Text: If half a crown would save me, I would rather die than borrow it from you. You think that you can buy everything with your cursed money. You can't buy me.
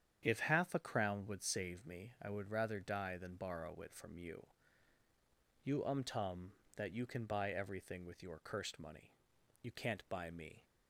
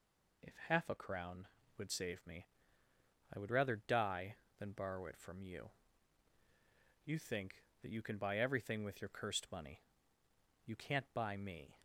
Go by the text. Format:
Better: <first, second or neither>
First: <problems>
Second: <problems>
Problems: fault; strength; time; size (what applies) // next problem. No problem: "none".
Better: second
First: starts louder than the rest; strong; until 1.2 s; 8.5 dB // says "umtum" for "think"; at 5.8 s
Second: none